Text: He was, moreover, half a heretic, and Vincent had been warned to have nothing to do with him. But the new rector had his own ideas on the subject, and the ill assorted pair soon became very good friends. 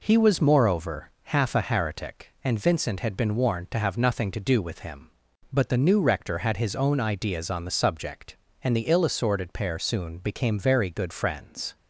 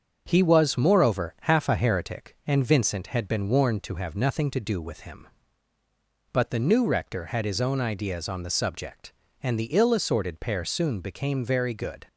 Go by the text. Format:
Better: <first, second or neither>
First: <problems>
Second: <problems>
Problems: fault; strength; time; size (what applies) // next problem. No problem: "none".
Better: first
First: none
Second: starts louder than the rest; until 1.2 s; 6.5 dB // stops before "friends"; at 12.0 s